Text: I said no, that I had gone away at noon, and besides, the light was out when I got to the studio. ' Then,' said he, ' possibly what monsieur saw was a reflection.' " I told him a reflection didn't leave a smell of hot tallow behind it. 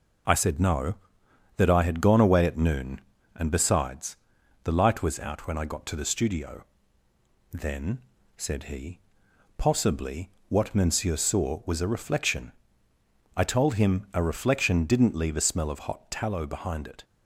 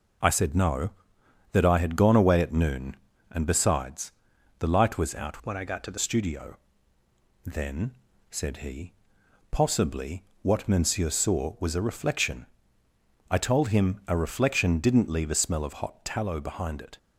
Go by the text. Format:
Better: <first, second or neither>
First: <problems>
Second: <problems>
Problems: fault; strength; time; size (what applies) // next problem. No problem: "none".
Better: first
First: pauses between "possibly" and "what"; slight; at 10.3 s; 0.18 s long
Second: changes voice from "when" to "the"; from 5.4 to 5.9 s; 0.5 s long // pauses between "possibly" and "what"; slight; at 10.2 s; 0.18 s long